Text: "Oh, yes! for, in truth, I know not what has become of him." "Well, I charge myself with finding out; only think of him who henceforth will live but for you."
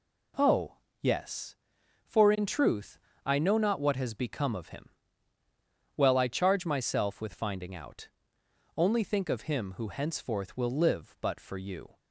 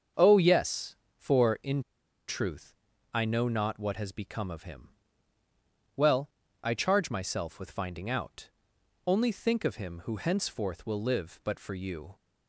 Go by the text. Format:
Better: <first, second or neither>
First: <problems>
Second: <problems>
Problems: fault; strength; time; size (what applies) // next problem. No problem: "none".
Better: first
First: none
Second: starts louder than the rest; until 1.3 s; 7 dB // pauses between "in" and "truth"; noticeable; at 1.8 s; 0.47 s long